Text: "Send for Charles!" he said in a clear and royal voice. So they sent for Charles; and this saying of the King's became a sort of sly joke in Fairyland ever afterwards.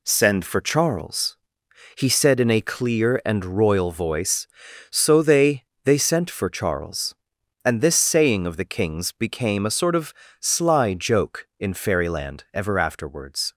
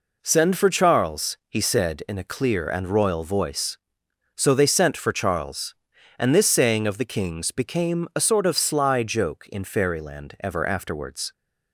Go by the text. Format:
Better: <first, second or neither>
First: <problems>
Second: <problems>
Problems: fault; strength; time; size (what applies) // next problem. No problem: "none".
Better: second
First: says "they" twice; at 5.8 s // pauses between "of" and "sly"; slight; at 10.1 s; 0.28 s long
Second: none